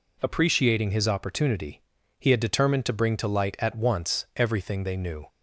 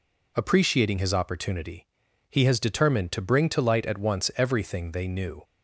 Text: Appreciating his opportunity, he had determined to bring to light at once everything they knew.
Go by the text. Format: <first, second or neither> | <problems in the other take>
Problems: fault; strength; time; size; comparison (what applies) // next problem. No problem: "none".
first | says "has" for "had"; at 2.4 s